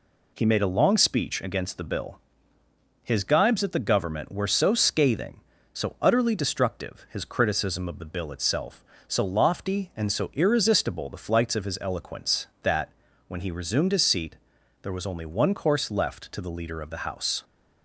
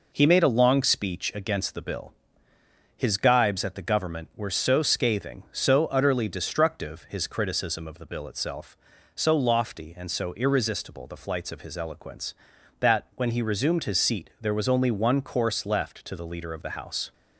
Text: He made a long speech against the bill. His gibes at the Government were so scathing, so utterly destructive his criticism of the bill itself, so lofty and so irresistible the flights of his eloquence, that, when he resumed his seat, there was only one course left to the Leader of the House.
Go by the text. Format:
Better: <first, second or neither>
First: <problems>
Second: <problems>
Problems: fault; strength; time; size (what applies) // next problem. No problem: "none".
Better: neither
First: none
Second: none